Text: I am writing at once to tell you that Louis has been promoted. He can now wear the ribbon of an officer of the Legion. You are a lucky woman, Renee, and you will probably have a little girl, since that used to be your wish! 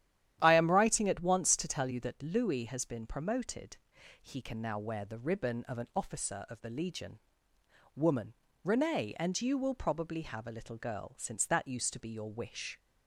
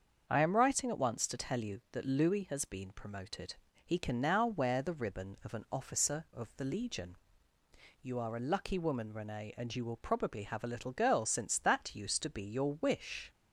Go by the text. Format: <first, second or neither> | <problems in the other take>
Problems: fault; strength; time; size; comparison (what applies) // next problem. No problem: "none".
second | starts louder than the rest; strong; until 1.4 s; 11 dB; also in the second // skips "You are a lucky"; at 7.5 s